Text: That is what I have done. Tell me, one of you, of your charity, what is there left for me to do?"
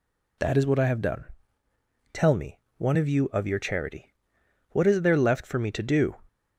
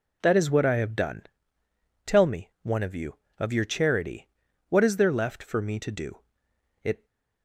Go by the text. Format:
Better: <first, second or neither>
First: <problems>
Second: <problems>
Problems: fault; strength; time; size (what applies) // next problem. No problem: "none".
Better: first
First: none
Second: goes on to say "It"; slight; from 6.8 s on; 0.22 s long